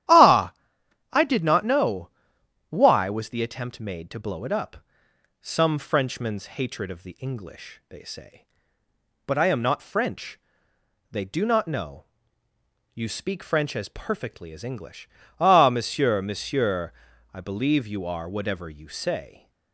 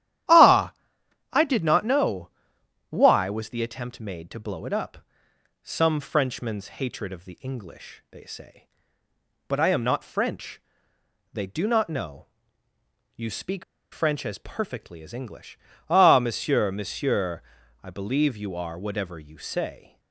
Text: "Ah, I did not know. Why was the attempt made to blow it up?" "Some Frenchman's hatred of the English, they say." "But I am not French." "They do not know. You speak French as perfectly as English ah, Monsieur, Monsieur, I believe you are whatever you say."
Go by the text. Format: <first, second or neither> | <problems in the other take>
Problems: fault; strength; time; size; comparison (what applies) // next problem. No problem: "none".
first | starts louder than the rest; strong; until 1.8 s; 11.5 dB; strong in the first // pauses between "speak" and "French"; slight; at 13.6 s; 0.29 s long // pauses between "English" and "ah"; slight; at 15.5 s; 0.32 s long; slight in the first